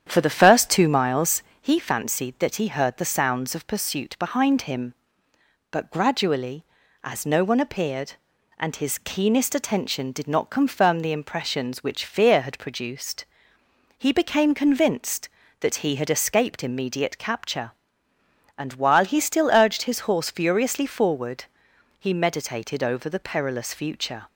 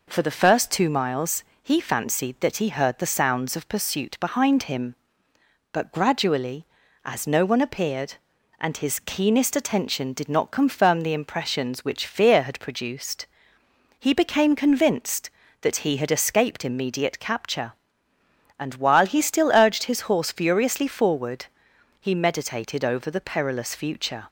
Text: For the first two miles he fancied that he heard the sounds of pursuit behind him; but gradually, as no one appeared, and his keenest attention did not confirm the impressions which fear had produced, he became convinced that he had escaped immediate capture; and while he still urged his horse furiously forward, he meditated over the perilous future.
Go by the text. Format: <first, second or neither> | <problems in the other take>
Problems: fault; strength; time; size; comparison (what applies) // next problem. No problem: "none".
second | starts louder than the rest; strong; until 1.8 s; 9 dB // pauses between "miles" and "he"; slight; at 1.4 s; 0.20 s long; slight in the second